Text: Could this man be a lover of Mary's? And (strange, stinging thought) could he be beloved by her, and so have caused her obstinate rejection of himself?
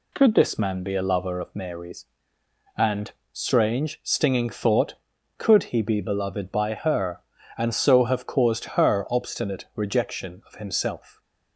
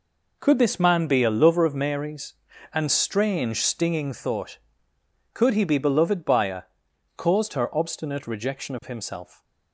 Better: first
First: none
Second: skips "and so have"; at 6.9 s

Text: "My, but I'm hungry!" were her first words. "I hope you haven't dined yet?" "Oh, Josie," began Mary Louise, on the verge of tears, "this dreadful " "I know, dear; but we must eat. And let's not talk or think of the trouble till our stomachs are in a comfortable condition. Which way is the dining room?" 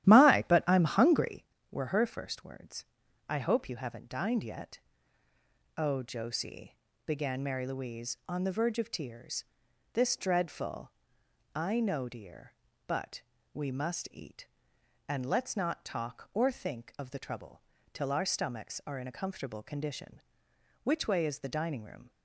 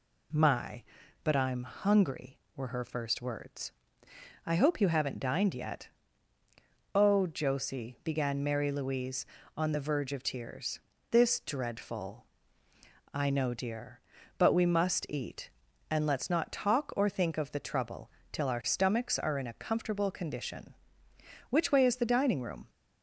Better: second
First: starts louder than the rest; strong; until 1.5 s; 12.5 dB // pauses between "but" and "we"; slight; at 13.2 s; 0.32 s long // pauses between "trouble" and "till"; slight; at 17.6 s; 0.32 s long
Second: pauses between "trouble" and "till"; slight; at 18.0 s; 0.22 s long

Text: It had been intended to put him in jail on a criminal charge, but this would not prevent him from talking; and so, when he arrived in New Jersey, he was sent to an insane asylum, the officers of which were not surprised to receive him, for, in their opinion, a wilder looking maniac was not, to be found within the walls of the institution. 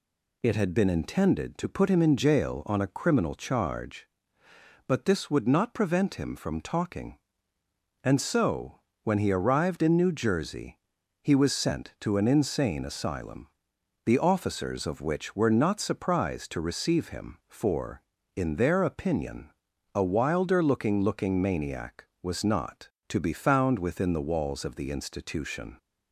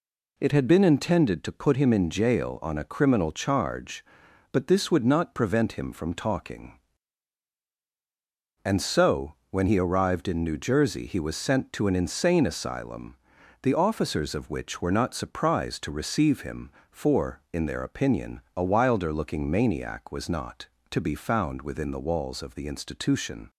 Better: second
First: says "looking" twice; at 21.0 s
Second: none

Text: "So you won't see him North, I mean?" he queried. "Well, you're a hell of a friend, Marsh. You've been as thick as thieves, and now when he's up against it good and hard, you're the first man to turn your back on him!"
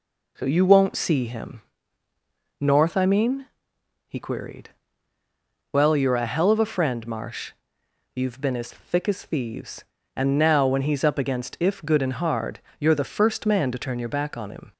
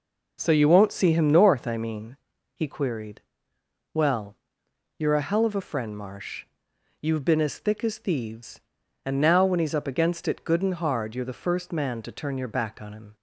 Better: second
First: pauses between "him" and "North"; noticeable; at 1.6 s; 0.98 s long // says "if" for "it"; at 11.5 s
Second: none

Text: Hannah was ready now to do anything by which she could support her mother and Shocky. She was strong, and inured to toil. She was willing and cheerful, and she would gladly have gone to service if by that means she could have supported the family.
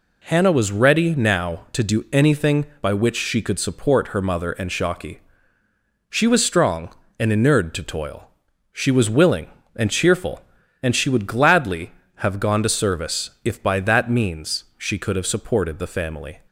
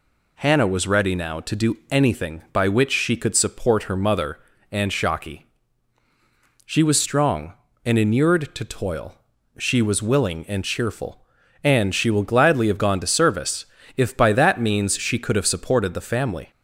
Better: first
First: none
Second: says "will" for "would"; at 12.1 s // pauses between "service" and "if"; slight; at 13.6 s; 0.32 s long

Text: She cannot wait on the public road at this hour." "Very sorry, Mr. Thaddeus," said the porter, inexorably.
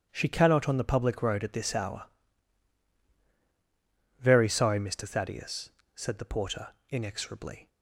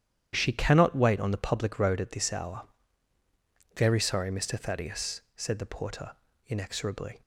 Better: second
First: starts louder than the rest; strong; until 1.1 s; 10.5 dB // skips "wait"; at 0.6 s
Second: starts louder than the rest; strong; until 1.3 s; 10.5 dB

